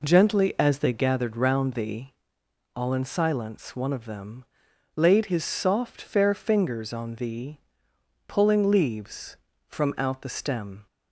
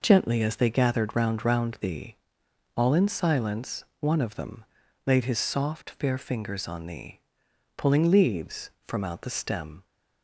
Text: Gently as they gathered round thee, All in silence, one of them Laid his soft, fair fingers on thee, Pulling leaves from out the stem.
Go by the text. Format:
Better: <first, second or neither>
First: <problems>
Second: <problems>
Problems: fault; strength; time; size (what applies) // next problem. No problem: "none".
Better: first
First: pauses between "them" and "Laid"; noticeable; at 4.4 s; 0.52 s long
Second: says "round" twice; at 1.4 s // pauses between "them" and "Laid"; at 4.6 s; 0.42 s long